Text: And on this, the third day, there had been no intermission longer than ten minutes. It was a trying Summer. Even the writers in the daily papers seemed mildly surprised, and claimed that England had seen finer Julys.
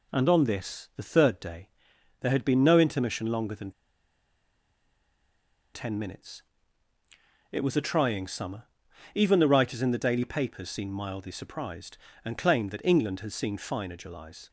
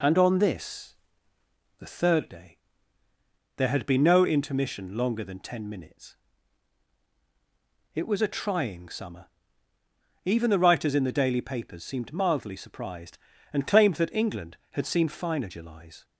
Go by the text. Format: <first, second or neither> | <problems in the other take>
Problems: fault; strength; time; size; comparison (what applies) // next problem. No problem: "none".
second | pauses between "than" and "ten"; strong; at 3.7 s; 2.0 s long